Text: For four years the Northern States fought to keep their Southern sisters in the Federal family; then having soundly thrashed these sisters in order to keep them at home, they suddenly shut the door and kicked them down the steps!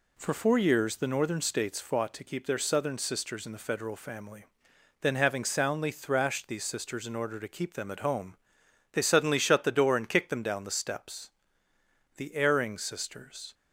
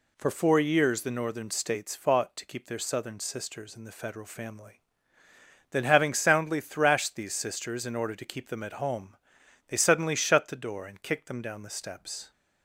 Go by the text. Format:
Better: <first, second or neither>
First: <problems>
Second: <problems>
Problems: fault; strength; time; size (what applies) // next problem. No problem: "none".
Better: second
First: goes on to say "The erring sisters"; from 12.1 s on; 1.3 s long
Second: none